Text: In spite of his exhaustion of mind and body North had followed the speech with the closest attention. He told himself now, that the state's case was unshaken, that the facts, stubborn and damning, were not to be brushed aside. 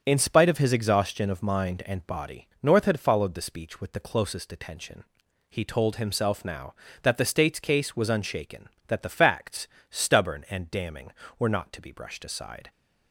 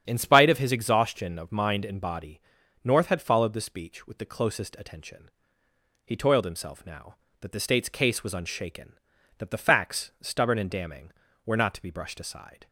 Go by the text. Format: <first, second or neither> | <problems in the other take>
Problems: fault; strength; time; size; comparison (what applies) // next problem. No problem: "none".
first | starts louder than the rest; strong; until 1.0 s; 8.5 dB; strong in the first // pauses between "body" and "North"; at 2.4 s; 0.42 s long // says "toiled" for "told"; at 6.1 s